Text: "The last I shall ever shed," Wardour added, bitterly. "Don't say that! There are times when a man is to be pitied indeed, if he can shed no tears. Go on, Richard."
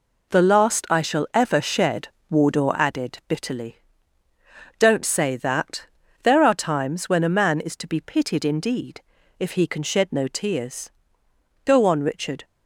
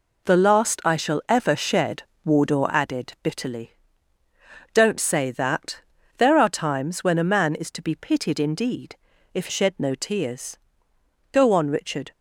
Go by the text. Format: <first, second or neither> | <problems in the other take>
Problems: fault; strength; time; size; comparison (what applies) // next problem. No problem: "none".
first | skips "he can"; at 9.4 s